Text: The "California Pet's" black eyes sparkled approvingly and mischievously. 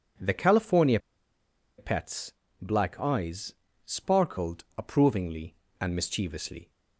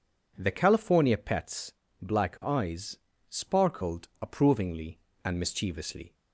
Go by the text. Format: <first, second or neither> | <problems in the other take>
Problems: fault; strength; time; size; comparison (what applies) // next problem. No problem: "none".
second | pauses between "California" and "Pet's"; noticeable; at 0.9 s; 0.80 s long // pauses between "Pet's" and "black"; slight; at 2.3 s; 0.28 s long; slight in the second // pauses between "eyes" and "sparkled"; slight; at 3.5 s; 0.30 s long; slight in the second